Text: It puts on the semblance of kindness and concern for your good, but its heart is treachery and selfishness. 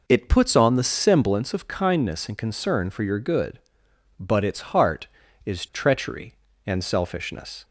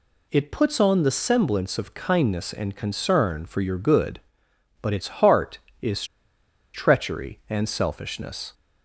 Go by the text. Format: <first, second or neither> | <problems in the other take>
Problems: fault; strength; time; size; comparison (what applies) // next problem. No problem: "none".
first | pauses between "is" and "treachery"; noticeable; at 6.0 s; 0.69 s long